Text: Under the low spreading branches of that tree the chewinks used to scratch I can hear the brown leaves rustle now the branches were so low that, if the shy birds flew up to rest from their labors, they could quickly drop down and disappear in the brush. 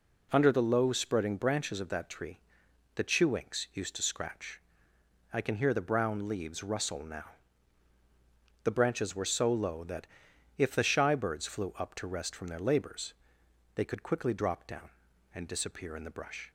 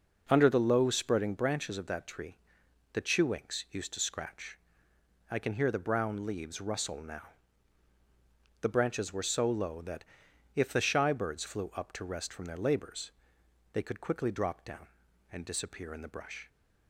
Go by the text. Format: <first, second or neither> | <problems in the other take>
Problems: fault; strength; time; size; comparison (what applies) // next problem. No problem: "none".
first | starts louder than the rest; noticeable; until 1.3 s; 5.5 dB // pauses between "tree" and "the"; noticeable; at 2.3 s; 0.56 s long; noticeable in the first // pauses between "scratch" and "I"; noticeable; at 4.5 s; 0.74 s long; noticeable in the first // pauses between "now" and "the"; strong; at 7.2 s; 1.4 s long; strong in the first